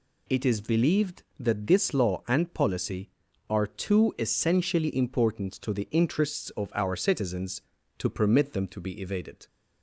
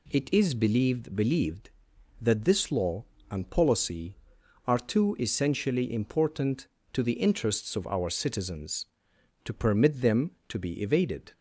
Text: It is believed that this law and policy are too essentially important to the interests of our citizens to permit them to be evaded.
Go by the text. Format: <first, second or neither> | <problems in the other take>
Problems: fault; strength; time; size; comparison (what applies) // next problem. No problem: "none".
first | says "believed" twice; at 1.1 s